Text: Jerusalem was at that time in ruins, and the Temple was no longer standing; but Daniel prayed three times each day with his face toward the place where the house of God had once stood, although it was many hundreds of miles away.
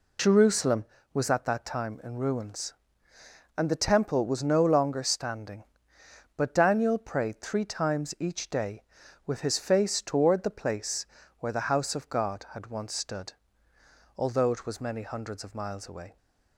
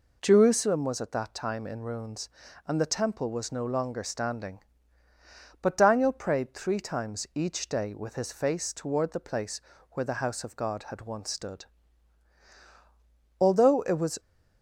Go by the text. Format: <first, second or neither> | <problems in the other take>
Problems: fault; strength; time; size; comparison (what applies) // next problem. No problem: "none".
first | pauses between "place" and "where"; slight; at 9.6 s; 0.30 s long; slight in the first // stops before "many hundreds of miles away"; at 14.1 s